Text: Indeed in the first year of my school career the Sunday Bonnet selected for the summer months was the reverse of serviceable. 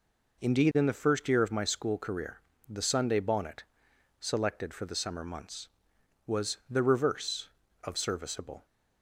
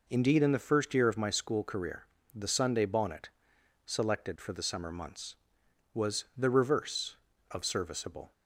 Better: neither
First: pauses between "career" and "the"; slight; at 2.4 s; 0.28 s long // pauses between "Bonnet" and "selected"; noticeable; at 3.6 s; 0.56 s long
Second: pauses between "career" and "the"; slight; at 2.0 s; 0.28 s long // pauses between "Bonnet" and "selected"; noticeable; at 3.2 s; 0.56 s long

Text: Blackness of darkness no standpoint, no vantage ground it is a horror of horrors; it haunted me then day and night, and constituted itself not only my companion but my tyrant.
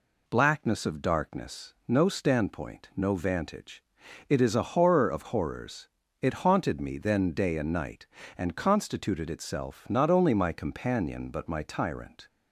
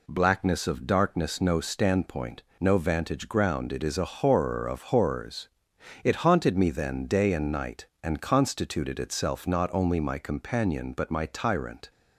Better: second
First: skips "ground"; at 4.0 s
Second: none

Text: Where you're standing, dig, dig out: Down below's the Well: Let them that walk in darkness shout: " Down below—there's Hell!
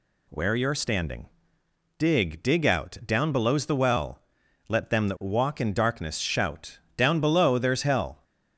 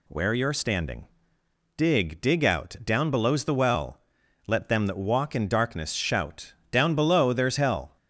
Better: neither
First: none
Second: none

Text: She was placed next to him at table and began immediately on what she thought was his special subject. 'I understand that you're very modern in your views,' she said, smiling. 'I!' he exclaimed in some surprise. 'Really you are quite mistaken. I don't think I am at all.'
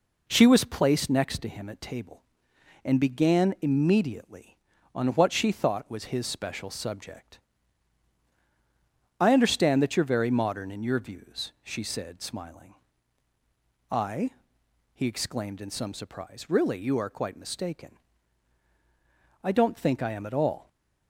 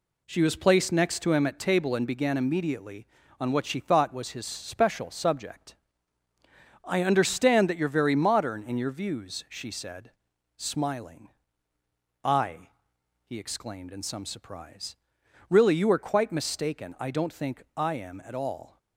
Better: neither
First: none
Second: none

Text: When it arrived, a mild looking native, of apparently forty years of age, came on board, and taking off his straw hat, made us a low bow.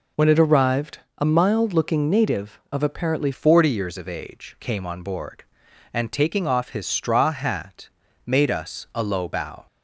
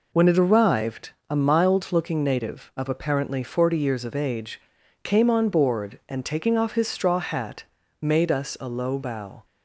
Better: second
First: changes voice at "forty"; from 3.3 s on; 6.3 s long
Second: none

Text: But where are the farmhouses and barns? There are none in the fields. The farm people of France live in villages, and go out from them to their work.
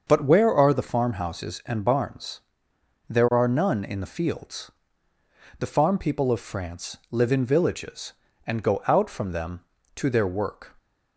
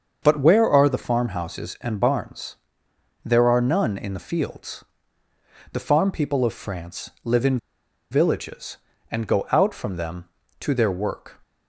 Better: first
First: starts louder than the rest; until 1.0 s; 6.5 dB // pauses between "France" and "live"; slight; at 6.9 s; 0.16 s long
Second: starts louder than the rest; until 1.2 s; 6.5 dB // pauses between "France" and "live"; slight; at 7.0 s; 0.16 s long // pauses between "in" and "villages"; noticeable; at 7.5 s; 0.53 s long

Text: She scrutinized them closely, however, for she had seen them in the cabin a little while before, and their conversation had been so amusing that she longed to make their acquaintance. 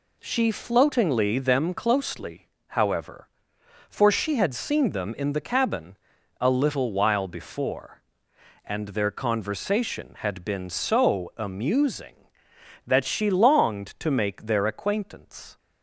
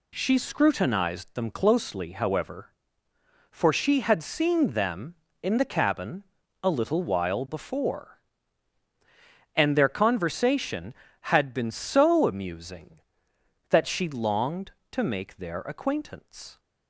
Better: second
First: says "floatingly" for "scrutinized"; at 0.5 s // pauses between "cabin" and "a"; at 5.9 s; 0.44 s long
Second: pauses between "cabin" and "a"; at 6.2 s; 0.40 s long

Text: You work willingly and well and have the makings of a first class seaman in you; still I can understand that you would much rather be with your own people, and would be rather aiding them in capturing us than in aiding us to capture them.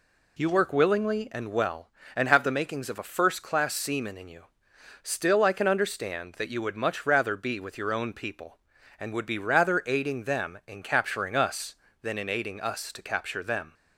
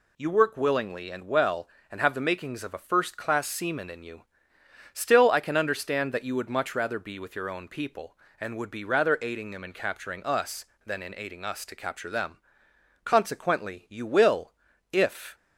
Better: first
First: none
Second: goes on to say "Consequently you will if"; strong; from 13.0 s on; 2.2 s long

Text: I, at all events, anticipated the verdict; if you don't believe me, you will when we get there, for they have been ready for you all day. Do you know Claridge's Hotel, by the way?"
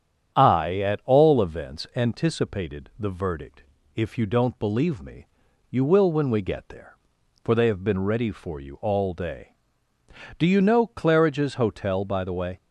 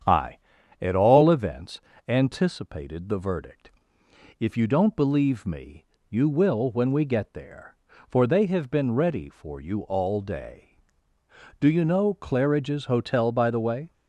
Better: neither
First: starts louder than the rest; strong; until 1.3 s; 9 dB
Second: starts louder than the rest; strong; until 1.4 s; 8.5 dB

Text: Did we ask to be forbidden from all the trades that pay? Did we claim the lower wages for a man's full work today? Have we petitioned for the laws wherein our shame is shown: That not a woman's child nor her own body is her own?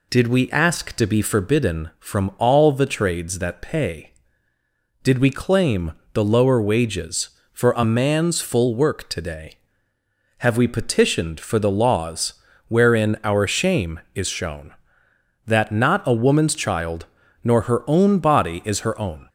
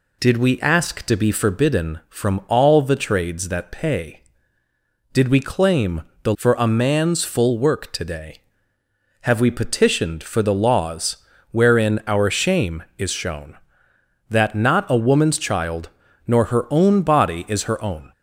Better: first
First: pauses between "claim" and "the"; slight; at 5.9 s; 0.22 s long // pauses between "laws" and "wherein"; slight; at 12.3 s; 0.34 s long // pauses between "child" and "nor"; at 17.0 s; 0.40 s long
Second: pauses between "claim" and "the"; slight; at 6.0 s; 0.22 s long // skips "lower wages"; at 6.3 s // pauses between "laws" and "wherein"; slight; at 11.1 s; 0.34 s long // pauses between "child" and "nor"; at 15.8 s; 0.40 s long

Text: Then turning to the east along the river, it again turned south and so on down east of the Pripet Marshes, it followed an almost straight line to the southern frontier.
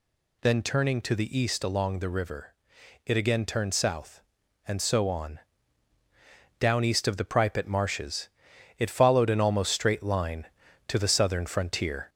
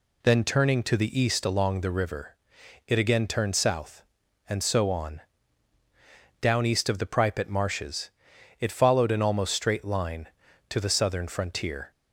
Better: second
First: gets louder; slight; throughout; 2.5 dB // pauses between "on" and "down"; at 5.3 s; 1.2 s long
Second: pauses between "on" and "down"; at 5.2 s; 1.2 s long

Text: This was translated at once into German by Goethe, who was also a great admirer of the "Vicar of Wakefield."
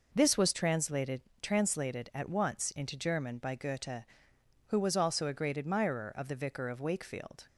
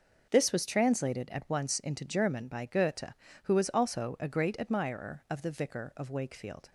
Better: second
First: says "translated" twice; at 1.4 s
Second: none

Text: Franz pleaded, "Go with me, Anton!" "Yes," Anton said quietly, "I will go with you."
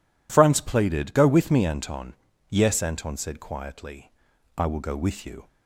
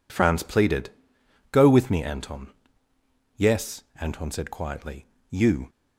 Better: first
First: none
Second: skips "I will go with"; at 5.1 s

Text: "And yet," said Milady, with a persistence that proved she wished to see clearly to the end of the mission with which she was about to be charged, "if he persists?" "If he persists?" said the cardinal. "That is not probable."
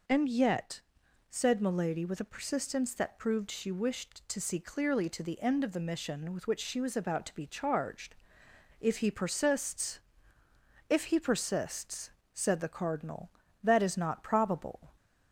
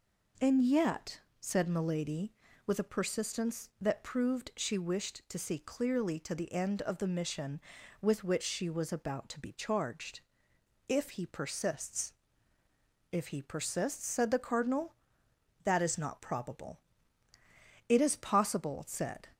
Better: first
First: none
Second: goes on to say "It is possible said"; from 17.8 s on; 1.4 s long

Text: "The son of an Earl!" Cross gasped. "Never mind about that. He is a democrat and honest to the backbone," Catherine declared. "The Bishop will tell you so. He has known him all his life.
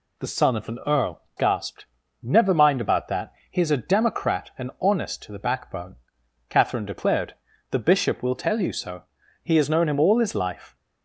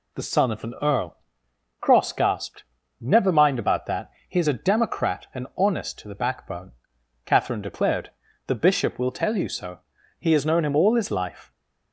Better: second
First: skips "Cross"; at 1.2 s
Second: none

